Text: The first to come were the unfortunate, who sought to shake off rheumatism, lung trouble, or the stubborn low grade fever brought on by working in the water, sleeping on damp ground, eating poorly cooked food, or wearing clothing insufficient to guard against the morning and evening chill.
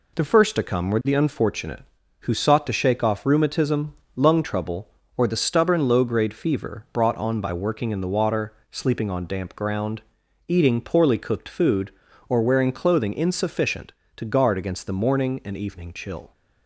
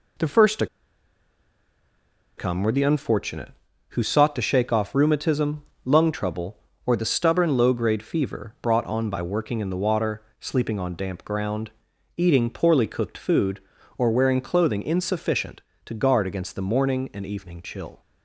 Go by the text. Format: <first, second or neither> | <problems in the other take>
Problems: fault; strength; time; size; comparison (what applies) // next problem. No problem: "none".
first | pauses between "to" and "come"; strong; at 0.6 s; 1.7 s long